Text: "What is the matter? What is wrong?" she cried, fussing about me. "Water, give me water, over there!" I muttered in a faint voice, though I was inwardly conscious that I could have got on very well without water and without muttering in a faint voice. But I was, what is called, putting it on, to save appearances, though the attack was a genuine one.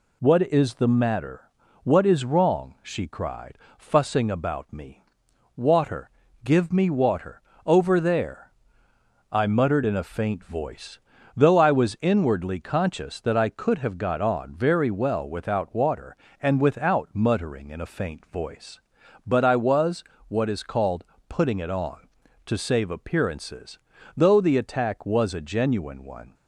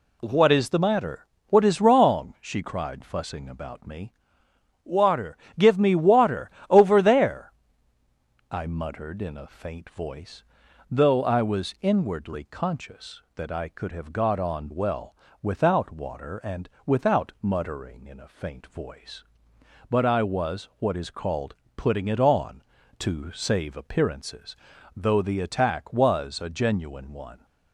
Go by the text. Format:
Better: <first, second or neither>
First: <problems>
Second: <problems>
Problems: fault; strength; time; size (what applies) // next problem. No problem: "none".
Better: first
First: none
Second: skips "very"; at 14.6 s // pauses between "well" and "without"; slight; at 15.1 s; 0.28 s long // pauses between "and" and "without"; slight; at 16.6 s; 0.20 s long